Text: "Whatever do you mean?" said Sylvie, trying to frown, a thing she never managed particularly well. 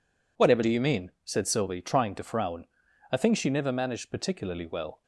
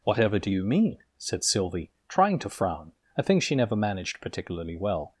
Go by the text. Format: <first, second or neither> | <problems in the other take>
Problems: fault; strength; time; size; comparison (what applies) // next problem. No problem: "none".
neither | none